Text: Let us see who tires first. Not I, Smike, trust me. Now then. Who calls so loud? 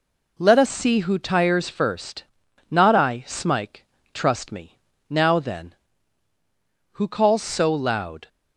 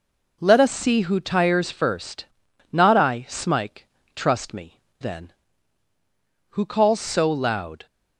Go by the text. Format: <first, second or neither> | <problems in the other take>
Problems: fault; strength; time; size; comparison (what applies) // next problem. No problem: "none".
first | skips "Now"; at 4.8 s